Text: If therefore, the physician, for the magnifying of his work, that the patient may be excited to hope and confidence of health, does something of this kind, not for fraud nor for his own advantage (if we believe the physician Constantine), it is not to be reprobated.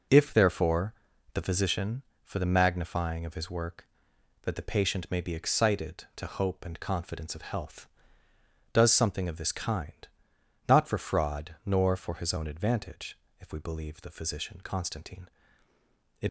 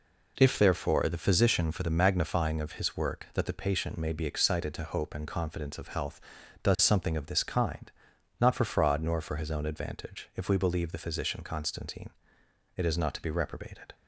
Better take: second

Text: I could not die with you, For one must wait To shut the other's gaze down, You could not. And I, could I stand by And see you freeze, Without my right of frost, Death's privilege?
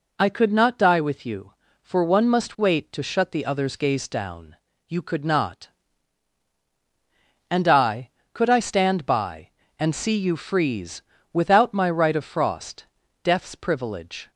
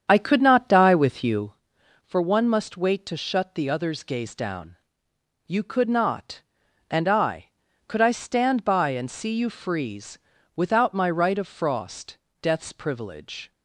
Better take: first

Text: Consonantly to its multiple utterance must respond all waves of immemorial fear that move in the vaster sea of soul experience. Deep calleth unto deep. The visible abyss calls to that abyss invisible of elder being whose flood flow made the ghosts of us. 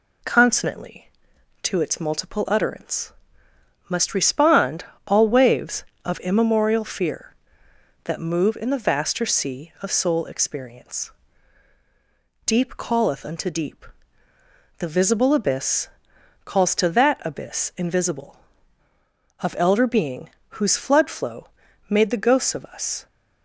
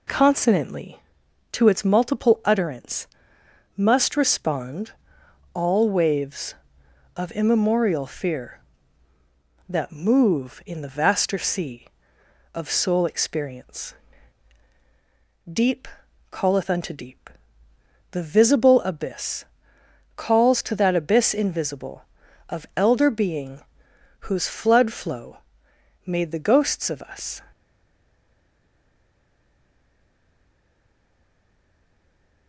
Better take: first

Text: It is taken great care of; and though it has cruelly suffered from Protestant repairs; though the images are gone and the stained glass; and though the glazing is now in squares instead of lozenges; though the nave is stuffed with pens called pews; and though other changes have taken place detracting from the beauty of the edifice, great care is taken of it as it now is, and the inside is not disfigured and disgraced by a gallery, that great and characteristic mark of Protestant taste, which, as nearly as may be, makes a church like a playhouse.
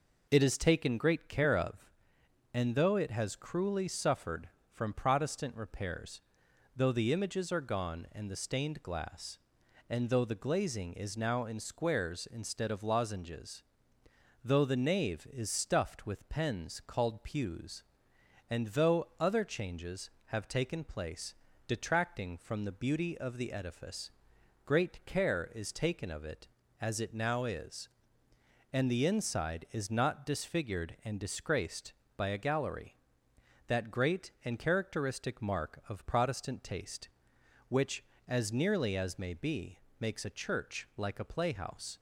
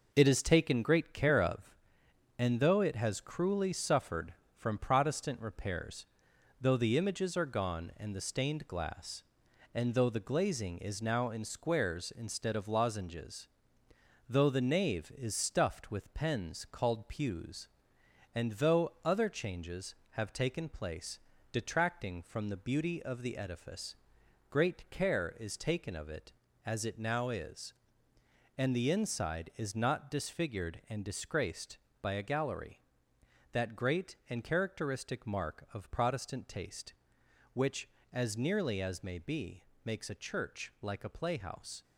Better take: first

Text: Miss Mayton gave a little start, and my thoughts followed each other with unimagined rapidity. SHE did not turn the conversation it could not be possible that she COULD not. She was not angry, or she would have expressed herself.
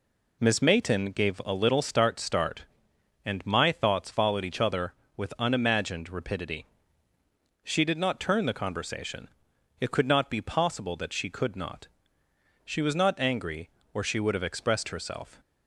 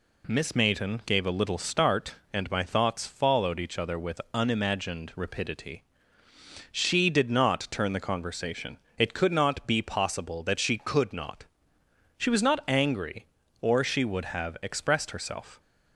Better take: second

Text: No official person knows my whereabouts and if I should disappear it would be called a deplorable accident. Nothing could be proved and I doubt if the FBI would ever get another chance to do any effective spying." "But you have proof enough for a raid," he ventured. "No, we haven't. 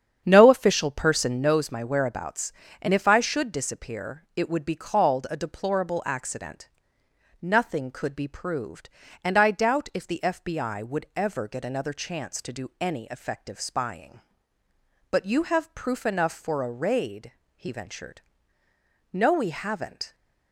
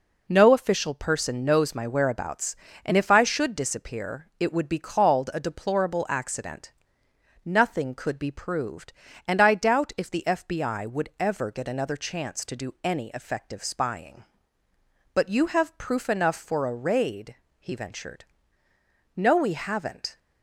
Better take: second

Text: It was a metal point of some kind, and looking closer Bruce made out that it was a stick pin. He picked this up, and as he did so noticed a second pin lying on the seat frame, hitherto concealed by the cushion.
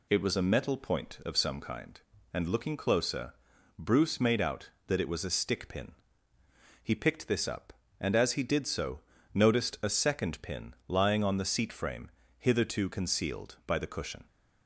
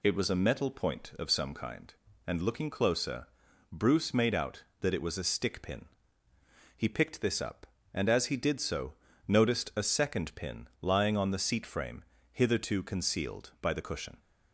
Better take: neither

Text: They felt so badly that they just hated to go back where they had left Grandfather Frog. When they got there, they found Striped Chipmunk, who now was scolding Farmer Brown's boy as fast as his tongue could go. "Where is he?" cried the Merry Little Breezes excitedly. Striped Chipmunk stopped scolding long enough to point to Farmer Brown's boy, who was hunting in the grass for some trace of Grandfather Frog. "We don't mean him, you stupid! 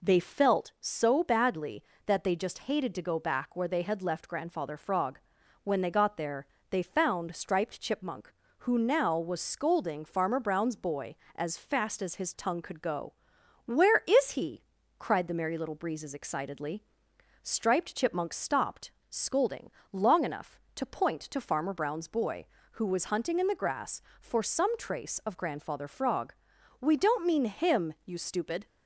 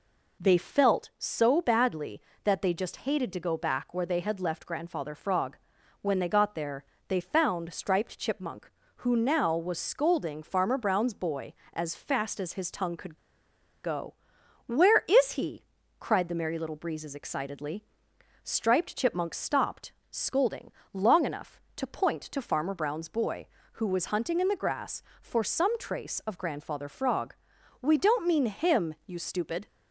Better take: first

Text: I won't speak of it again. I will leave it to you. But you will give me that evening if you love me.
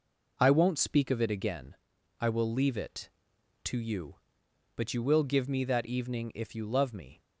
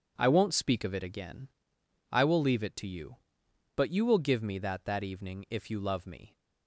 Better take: first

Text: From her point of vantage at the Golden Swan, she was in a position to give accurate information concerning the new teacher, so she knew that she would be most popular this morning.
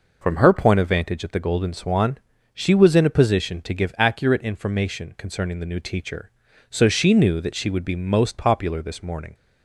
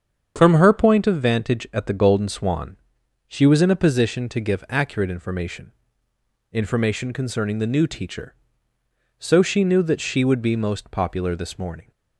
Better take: first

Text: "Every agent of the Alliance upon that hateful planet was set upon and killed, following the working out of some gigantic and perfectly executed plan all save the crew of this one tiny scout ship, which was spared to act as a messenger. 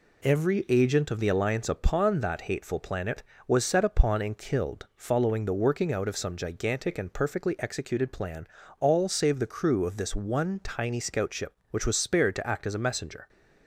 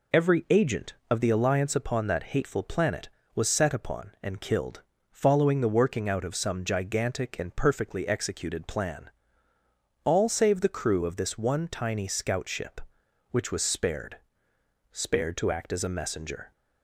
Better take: first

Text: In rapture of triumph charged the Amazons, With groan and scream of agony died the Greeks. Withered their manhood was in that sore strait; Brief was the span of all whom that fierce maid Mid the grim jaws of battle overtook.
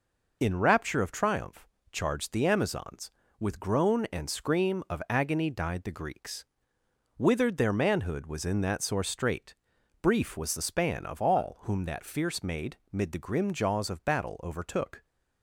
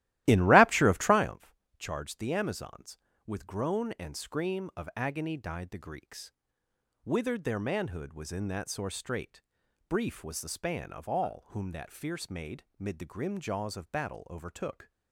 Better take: first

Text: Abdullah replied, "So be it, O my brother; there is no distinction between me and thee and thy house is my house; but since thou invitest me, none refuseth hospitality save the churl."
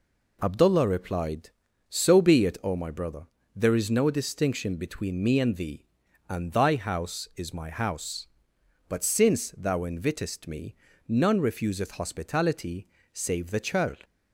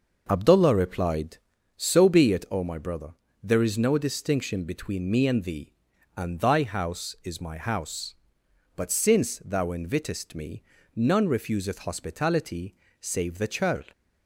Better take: first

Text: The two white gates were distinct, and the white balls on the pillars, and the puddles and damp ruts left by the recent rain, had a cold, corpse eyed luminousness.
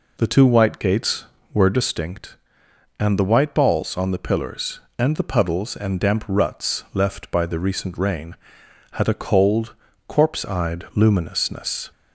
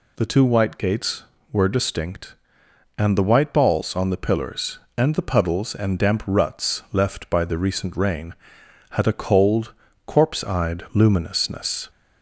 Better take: second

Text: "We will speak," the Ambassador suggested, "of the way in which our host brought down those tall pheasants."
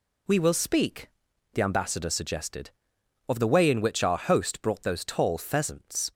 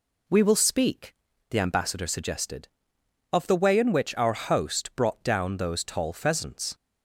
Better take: second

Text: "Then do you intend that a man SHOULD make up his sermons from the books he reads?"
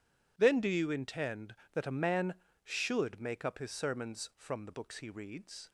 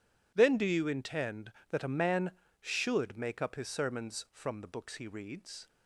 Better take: neither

